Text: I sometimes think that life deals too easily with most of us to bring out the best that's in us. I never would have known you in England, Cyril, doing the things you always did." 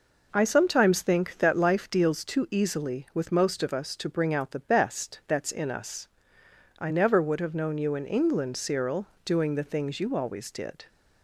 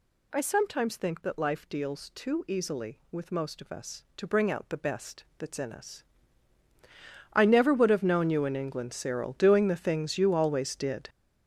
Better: first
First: none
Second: gets louder; strong; throughout; 10 dB // pauses between "best" and "that's"; slight; at 5.2 s; 0.15 s long

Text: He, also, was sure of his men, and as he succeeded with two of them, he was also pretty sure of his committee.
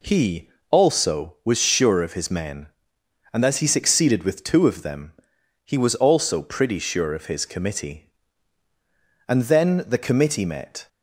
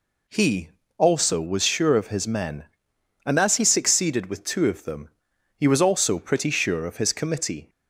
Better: second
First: goes on to say "And then the committee met"; from 9.2 s on; 1.6 s long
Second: none

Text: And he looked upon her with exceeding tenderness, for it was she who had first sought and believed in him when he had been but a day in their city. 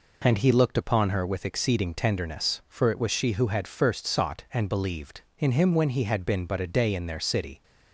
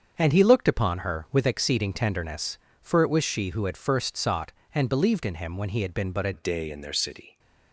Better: first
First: none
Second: starts louder than the rest; until 1.1 s; 7 dB // changes voice at "day"; from 6.3 s on; 1.0 s long

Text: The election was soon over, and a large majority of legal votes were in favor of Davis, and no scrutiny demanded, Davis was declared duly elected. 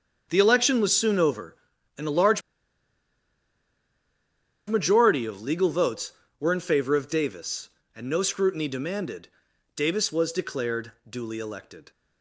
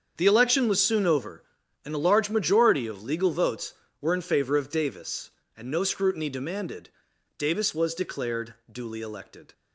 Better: second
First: starts louder than the rest; until 1.3 s; 7 dB // pauses between "large" and "majority"; strong; at 2.4 s; 2.2 s long // pauses between "declared" and "duly"; slight; at 10.9 s; 0.16 s long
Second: starts louder than the rest; until 1.1 s; 7 dB // pauses between "declared" and "duly"; slight; at 8.5 s; 0.16 s long

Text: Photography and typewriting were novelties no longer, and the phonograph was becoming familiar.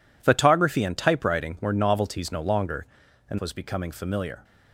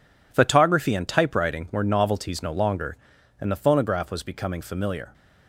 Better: second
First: skips "the phonograph"; at 3.3 s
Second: none

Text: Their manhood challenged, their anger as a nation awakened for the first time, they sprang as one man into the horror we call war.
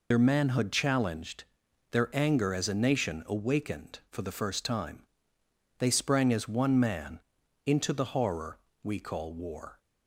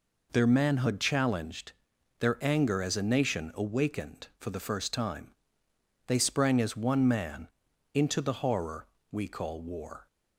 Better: second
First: loses the start of "Their"; at 0.1 s; 70 ms // pauses between "man" and "into"; at 7.2 s; 0.44 s long // pauses between "horror" and "we"; slight; at 8.5 s; 0.24 s long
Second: pauses between "man" and "into"; at 7.4 s; 0.44 s long // pauses between "horror" and "we"; slight; at 8.8 s; 0.24 s long

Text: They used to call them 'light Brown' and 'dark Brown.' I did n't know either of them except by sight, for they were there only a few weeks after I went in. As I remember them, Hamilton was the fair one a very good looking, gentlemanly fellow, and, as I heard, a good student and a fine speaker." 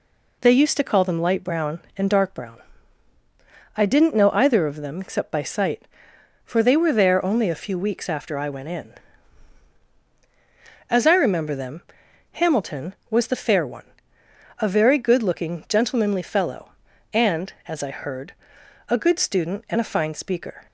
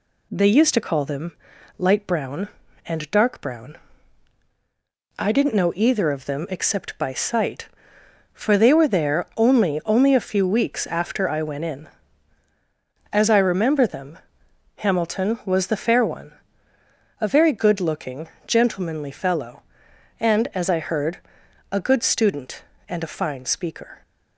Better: first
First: pauses between "one" and "a"; noticeable; at 13.8 s; 0.72 s long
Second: pauses between "them" and "light"; noticeable; at 1.3 s; 0.46 s long // says "only" twice; at 9.8 s // pauses between "one" and "a"; noticeable; at 16.3 s; 0.88 s long

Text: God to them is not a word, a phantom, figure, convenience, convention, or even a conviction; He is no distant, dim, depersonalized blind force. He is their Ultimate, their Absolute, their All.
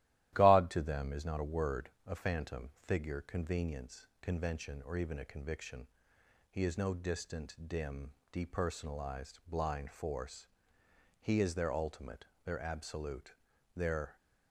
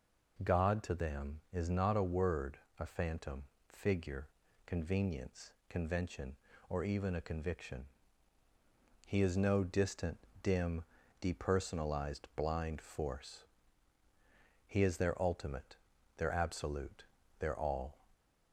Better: second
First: starts louder than the rest; strong; until 1.3 s; 14 dB // stops before "All"; at 14.1 s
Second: none

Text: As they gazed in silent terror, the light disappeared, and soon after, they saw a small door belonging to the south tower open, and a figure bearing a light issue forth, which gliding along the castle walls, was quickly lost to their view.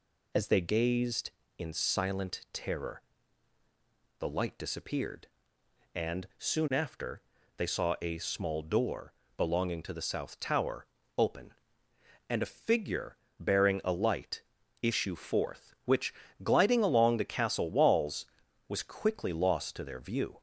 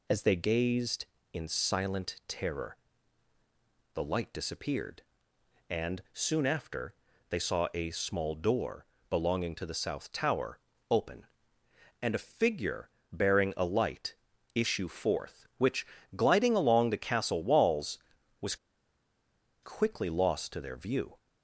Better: first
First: pauses between "door" and "belonging"; slight; at 9.1 s; 0.24 s long // pauses between "tower" and "open"; slight; at 10.8 s; 0.30 s long // pauses between "figure" and "bearing"; slight; at 13.1 s; 0.24 s long // pauses between "light" and "issue"; at 14.4 s; 0.42 s long // pauses between "which" and "gliding"; slight; at 16.1 s; 0.30 s long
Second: pauses between "door" and "belonging"; slight; at 8.8 s; 0.24 s long // pauses between "tower" and "open"; slight; at 10.5 s; 0.30 s long // pauses between "figure" and "bearing"; slight; at 12.8 s; 0.24 s long // pauses between "light" and "issue"; at 14.1 s; 0.42 s long // pauses between "which" and "gliding"; slight; at 15.8 s; 0.30 s long // pauses between "was" and "quickly"; at 18.5 s; 1.0 s long

